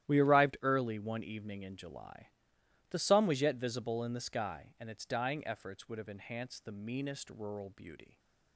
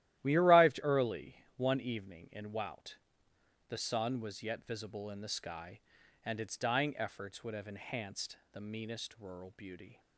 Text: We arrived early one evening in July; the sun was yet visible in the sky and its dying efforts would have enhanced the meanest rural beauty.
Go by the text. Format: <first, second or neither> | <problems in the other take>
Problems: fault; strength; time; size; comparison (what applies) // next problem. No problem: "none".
first | starts louder than the rest; strong; until 1.2 s; 13.5 dB; strong in the first // pauses between "early" and "one"; slight; at 1.3 s; 0.22 s long // says "Wout" for "July"; at 2.5 s